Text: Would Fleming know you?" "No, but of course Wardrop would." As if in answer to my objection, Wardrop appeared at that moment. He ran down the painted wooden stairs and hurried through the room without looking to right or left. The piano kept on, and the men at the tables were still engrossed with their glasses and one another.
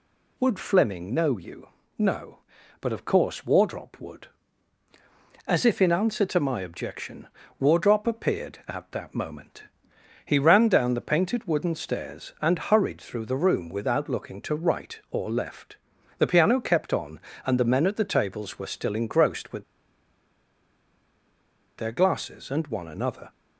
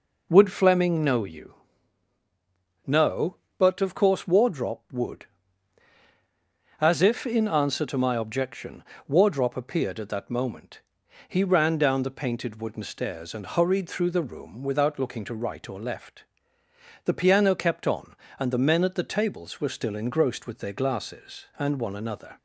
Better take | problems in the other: second | pauses between "with" and "their"; strong; at 19.6 s; 2.1 s long

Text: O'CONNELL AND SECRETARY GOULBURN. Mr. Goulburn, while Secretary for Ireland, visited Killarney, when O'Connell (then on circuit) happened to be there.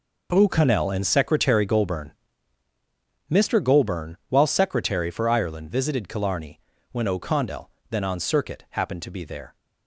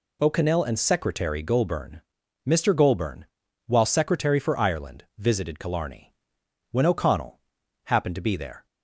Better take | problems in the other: first | skips "then on circuit"; at 7.6 s

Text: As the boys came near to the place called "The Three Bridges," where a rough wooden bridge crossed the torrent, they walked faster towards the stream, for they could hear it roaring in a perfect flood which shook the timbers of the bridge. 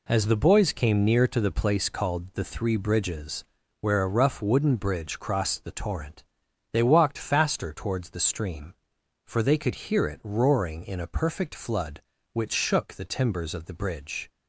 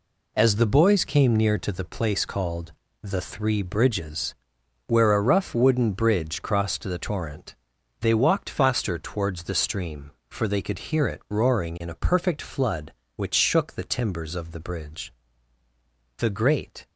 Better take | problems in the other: first | pauses between "called" and "The"; slight; at 2.7 s; 0.28 s long // goes on to say "The great"; noticeable; from 16.1 s on; 0.66 s long

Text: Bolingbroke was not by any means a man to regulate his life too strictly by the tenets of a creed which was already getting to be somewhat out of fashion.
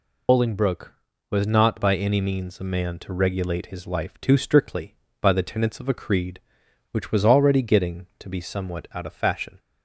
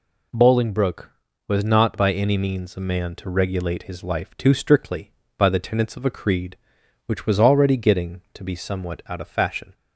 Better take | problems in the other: second | loses the start of "Bolingbroke"; at 0.2 s; 145 ms

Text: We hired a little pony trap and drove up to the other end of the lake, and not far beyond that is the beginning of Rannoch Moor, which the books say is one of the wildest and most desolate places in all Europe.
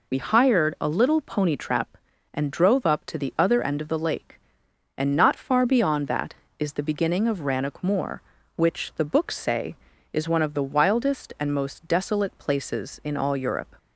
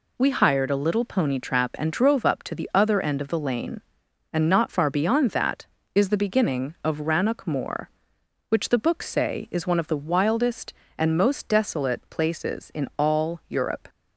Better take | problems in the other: first | says "lane" for "lake"; at 3.3 s

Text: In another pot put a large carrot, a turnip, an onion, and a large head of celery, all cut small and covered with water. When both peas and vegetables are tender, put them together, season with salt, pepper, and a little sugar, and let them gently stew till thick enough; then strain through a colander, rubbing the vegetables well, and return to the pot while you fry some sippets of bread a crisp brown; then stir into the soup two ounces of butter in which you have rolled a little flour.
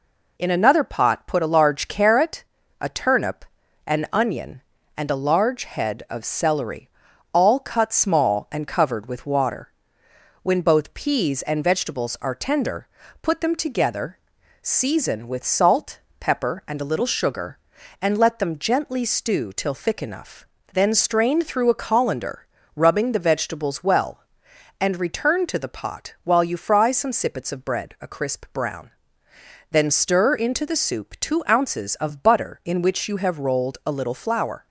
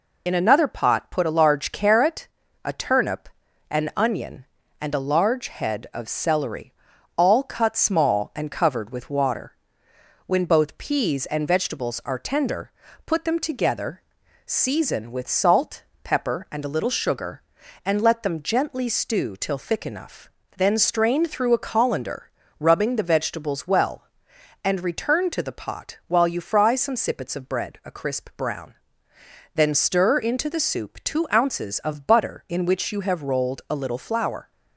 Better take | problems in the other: first | loses the start of "In"; at 0.2 s; 35 ms

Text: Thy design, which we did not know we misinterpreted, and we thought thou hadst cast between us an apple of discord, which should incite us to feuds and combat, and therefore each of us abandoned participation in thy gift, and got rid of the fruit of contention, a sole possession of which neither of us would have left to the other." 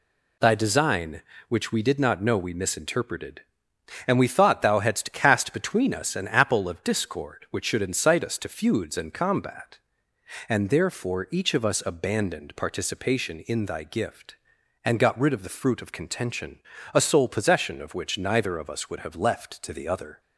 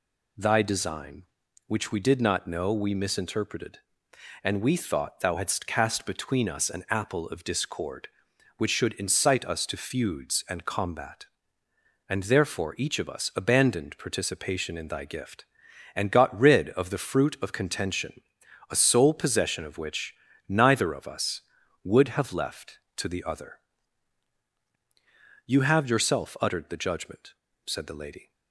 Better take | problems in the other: first | pauses between "which" and "neither"; slight; at 20.1 s; 0.32 s long // goes on to say "You have yourself uttered the judgment said the lady"; strong; from 25.4 s on; 2.8 s long

